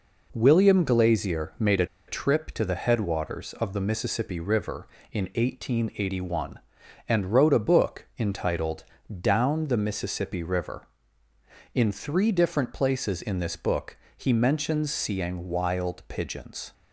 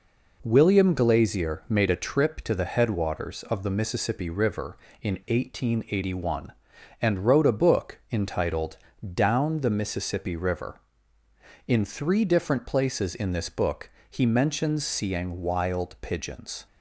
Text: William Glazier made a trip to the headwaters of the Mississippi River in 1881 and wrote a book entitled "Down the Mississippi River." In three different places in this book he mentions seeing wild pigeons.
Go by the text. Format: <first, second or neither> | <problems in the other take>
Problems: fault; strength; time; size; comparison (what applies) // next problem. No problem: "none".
second | pauses between "a" and "trip"; slight; at 1.8 s; 0.23 s long // pauses between "entitled" and "Down"; at 8.8 s; 0.38 s long; also in the second // pauses between "book" and "he"; slight; at 13.9 s; 0.22 s long; slight in the second